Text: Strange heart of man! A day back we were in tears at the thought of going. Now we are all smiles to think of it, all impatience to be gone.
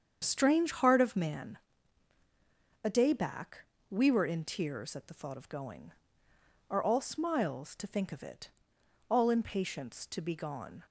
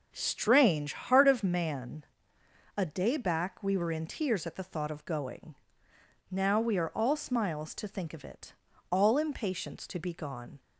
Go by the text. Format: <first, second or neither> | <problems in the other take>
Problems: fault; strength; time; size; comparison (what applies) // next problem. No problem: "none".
second | starts louder than the rest; strong; until 1.2 s; 7.5 dB // pauses between "back" and "we"; slight; at 3.6 s; 0.26 s long // skips "Now we"; at 6.3 s